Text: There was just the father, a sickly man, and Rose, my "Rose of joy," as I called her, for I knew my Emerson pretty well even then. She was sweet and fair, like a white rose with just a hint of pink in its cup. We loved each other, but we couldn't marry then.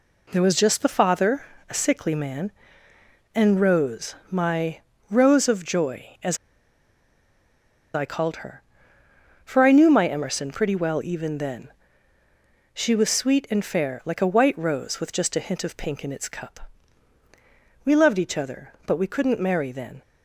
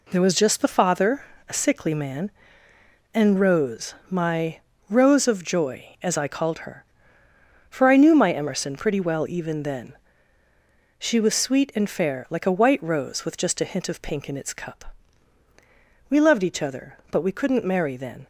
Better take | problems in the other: second | pauses between "my" and "Rose"; slight; at 4.8 s; 0.28 s long; slight in the second // pauses between "as" and "I"; strong; at 6.3 s; 1.5 s long

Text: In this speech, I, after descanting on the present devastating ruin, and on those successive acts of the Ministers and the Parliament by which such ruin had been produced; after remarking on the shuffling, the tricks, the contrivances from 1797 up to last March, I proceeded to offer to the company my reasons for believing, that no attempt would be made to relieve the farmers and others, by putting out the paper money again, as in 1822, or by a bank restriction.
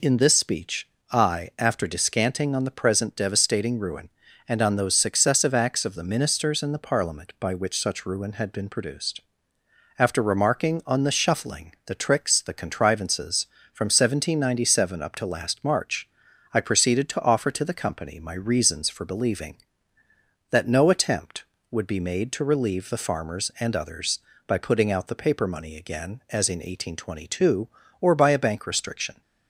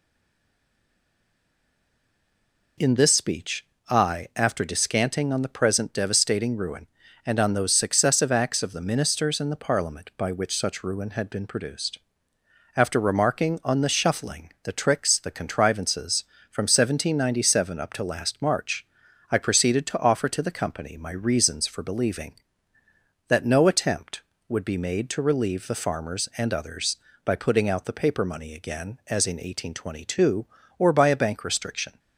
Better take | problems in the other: first | stays silent before the first word; strong; until 2.7 s; 2.7 s long

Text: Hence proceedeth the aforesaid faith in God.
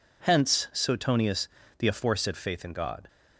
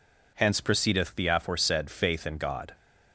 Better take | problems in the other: second | says "suetonius" for "proceedeth"; at 0.7 s

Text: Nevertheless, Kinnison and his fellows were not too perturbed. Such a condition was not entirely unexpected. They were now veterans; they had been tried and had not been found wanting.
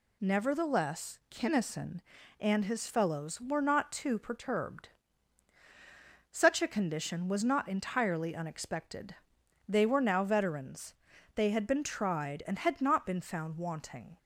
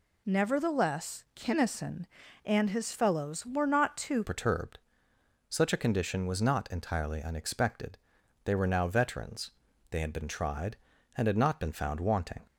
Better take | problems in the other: first | changes voice at "perturbed"; from 4.2 s on; 8.2 s long

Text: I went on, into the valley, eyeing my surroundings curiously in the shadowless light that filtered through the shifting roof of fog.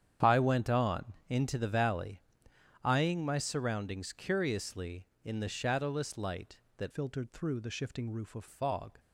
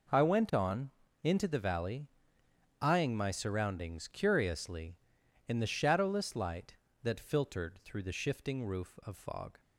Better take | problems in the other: second | starts louder than the rest; strong; until 1.4 s; 9 dB // changes voice from "filtered" to "of"; from 6.9 to 8.4 s; 1.5 s long

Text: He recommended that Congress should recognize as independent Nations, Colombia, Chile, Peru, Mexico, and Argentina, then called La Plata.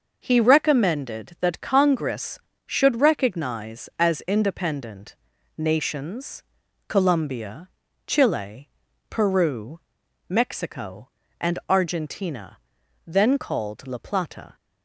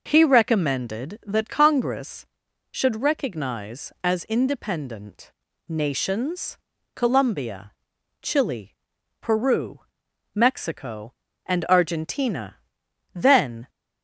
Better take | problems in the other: first | pauses between "independent" and "Nations"; at 5.3 s; 0.38 s long; also in the first // stops before "called La Plata"; at 13.6 s

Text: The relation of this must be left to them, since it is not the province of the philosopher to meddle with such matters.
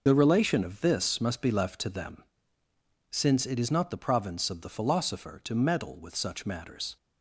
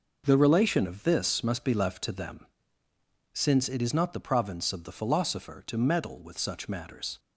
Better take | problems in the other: second | loses the start of "The"; at 0.0 s; 50 ms

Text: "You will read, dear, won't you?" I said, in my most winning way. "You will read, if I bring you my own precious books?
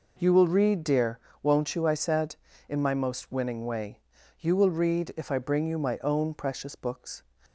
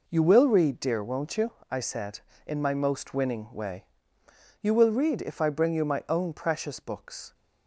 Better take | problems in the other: neither | none

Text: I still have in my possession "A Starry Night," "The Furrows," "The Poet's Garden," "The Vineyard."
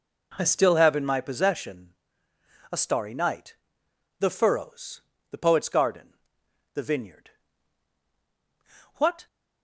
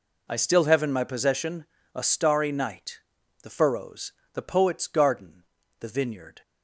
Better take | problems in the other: second | pauses between "possession" and "A"; noticeable; at 1.9 s; 0.78 s long; slight in the second // goes on to say "What"; slight; from 8.9 s on; 0.32 s long

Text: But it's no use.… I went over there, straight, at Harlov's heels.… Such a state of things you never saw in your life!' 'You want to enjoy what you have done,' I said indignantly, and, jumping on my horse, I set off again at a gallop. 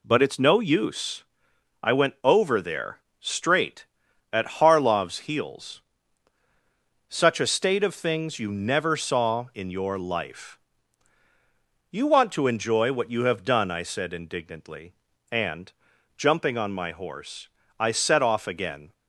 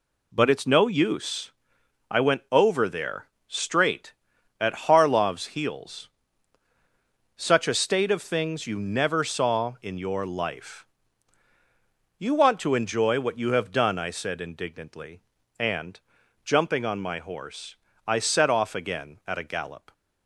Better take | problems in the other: second | stops before "at a gallop"; at 18.9 s

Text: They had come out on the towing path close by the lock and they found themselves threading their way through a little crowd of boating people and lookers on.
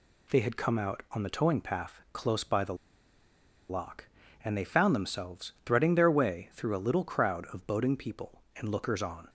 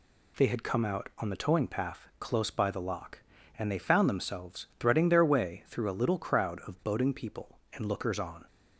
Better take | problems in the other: second | pauses between "the" and "lock"; noticeable; at 2.7 s; 0.94 s long

